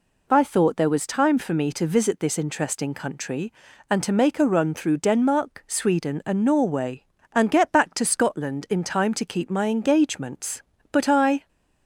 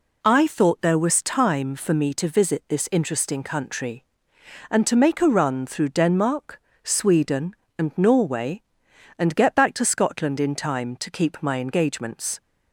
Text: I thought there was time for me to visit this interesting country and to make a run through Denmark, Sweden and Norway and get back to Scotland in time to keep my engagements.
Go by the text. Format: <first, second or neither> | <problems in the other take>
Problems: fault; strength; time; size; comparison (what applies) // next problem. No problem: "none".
second | goes on to say "But I"; from 10.9 s on; 0.56 s long